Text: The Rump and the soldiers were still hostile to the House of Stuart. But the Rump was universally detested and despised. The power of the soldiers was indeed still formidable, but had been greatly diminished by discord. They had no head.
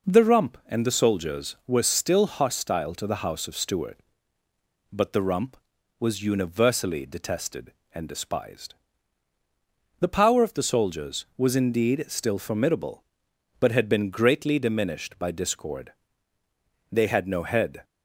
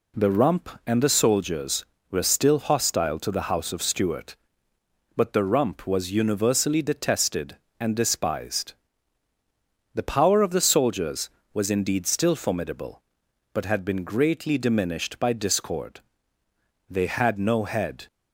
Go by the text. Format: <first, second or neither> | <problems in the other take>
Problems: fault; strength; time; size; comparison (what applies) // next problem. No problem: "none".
neither | none